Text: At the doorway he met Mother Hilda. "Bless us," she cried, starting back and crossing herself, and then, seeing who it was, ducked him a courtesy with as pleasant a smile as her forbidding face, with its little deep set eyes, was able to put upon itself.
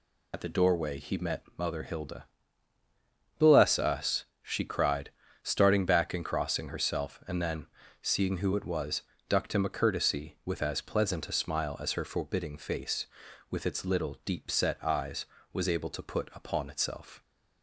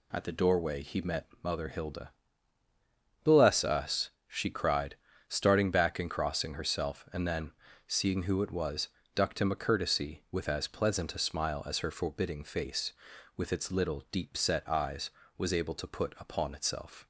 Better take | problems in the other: second | loses the start of "At"; at 0.3 s; 70 ms

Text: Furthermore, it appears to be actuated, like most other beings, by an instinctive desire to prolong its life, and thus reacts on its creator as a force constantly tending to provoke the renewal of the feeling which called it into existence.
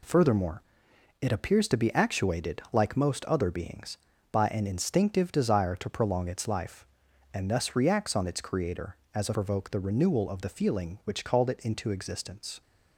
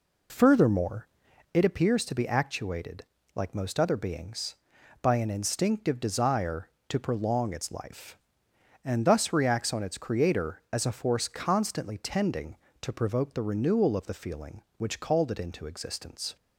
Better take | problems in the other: second | skips "force constantly tending to"; at 9.3 s

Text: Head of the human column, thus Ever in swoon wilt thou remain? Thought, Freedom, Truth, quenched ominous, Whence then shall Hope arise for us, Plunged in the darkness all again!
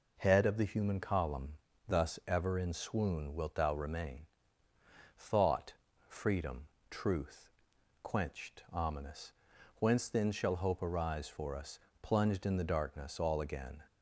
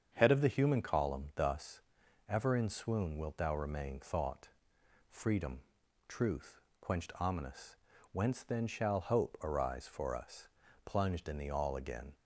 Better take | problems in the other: first | starts louder than the rest; strong; until 1.1 s; 7.5 dB // pauses between "thus" and "Ever"; noticeable; at 1.7 s; 0.48 s long // skips "darkness"; at 11.4 s

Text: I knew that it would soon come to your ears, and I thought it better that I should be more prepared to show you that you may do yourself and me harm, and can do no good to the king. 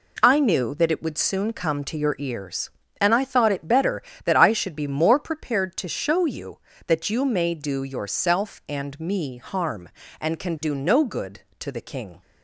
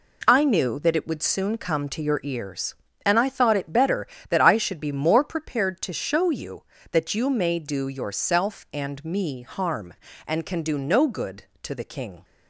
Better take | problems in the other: neither | none

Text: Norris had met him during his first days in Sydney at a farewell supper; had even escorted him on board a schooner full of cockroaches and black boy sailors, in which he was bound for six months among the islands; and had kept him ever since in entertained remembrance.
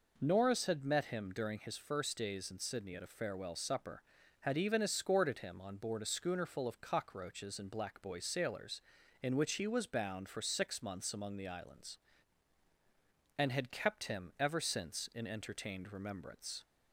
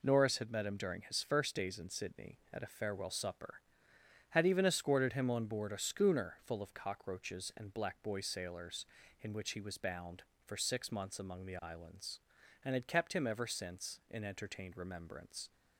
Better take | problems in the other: neither | none

